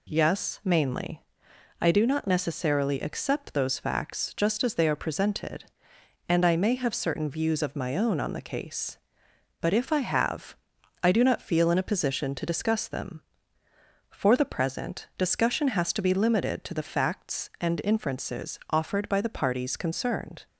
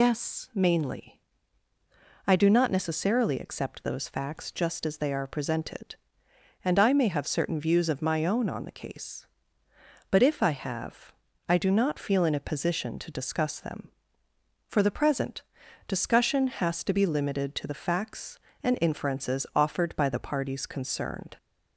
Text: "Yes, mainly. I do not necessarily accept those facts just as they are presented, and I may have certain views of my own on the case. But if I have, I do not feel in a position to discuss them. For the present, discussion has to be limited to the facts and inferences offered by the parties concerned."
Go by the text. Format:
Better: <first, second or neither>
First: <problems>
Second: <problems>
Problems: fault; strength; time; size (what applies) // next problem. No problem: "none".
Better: first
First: none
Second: loses the start of "Yes"; at 0.0 s; 135 ms